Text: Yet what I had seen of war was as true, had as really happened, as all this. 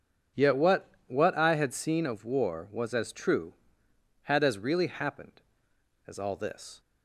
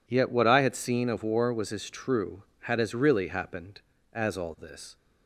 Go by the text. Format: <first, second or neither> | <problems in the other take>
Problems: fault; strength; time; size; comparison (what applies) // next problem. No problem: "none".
second | says "what" twice; at 1.0 s